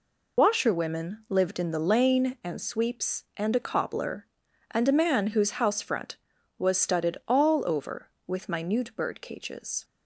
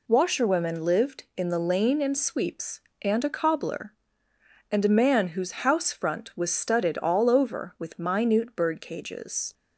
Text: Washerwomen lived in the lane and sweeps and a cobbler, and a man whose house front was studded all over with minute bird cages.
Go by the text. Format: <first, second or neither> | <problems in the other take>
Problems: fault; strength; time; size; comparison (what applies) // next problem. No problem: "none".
second | loses the start of "Washerwomen"; at 0.3 s; 35 ms